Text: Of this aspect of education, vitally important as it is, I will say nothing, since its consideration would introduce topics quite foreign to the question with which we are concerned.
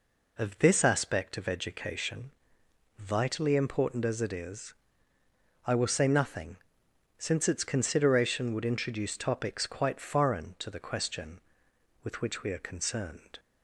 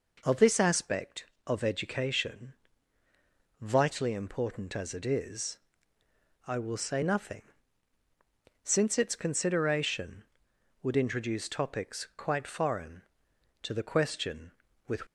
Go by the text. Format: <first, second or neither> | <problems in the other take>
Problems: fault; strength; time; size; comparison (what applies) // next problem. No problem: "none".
first | stops before "which we are concerned"; at 15.0 s